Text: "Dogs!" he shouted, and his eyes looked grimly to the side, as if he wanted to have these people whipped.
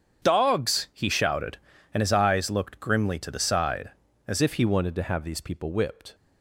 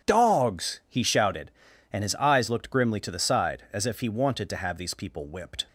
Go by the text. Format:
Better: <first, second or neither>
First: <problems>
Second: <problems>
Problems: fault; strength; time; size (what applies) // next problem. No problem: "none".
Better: second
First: starts louder than the rest; strong; until 1.2 s; 8 dB // changes voice at "if"; from 4.4 s on; 1.7 s long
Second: starts louder than the rest; strong; until 1.1 s; 9 dB